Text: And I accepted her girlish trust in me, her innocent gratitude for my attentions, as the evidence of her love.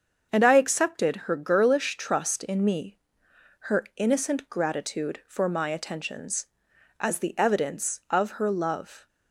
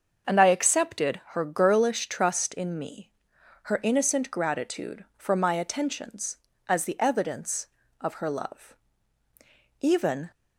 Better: first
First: starts louder than the rest; until 1.3 s; 6.5 dB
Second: starts louder than the rest; until 1.3 s; 6.5 dB // goes on to say "Even"; from 9.8 s on; 0.50 s long

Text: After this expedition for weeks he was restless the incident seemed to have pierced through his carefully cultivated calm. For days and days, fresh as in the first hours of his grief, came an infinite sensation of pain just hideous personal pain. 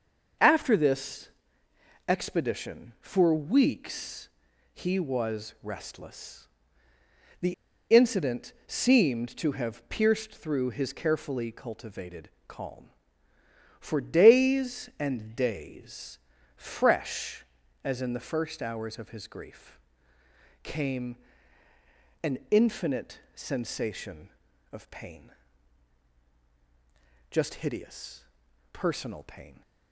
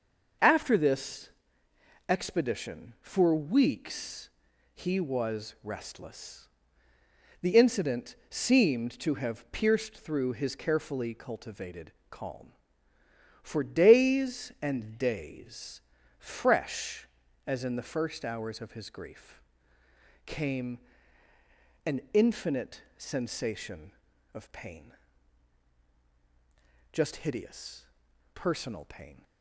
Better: second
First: starts louder than the rest; until 2.2 s; 6.5 dB // pauses between "this" and "expedition"; noticeable; at 1.2 s; 0.78 s long // pauses between "weeks" and "he"; at 4.2 s; 0.44 s long // pauses between "restless" and "the"; noticeable; at 6.4 s; 0.96 s long // pauses between "the" and "incident"; at 7.5 s; 0.39 s long // pauses between "cultivated" and "calm"; slight; at 12.2 s; 0.16 s long // pauses between "came" and "an"; at 21.1 s; 1.0 s long // pauses between "pain" and "just"; strong; at 25.3 s; 1.9 s long // pauses between "hideous" and "personal"; noticeable; at 28.2 s; 0.50 s long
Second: starts louder than the rest; until 2.2 s; 6.5 dB // pauses between "this" and "expedition"; noticeable; at 1.2 s; 0.78 s long // pauses between "weeks" and "he"; at 4.2 s; 0.44 s long // pauses between "restless" and "the"; noticeable; at 6.4 s; 0.96 s long // pauses between "cultivated" and "calm"; slight; at 11.9 s; 0.16 s long // pauses between "came" and "an"; at 20.7 s; 1.0 s long // pauses between "pain" and "just"; strong; at 24.9 s; 1.9 s long // pauses between "hideous" and "personal"; noticeable; at 27.8 s; 0.50 s long

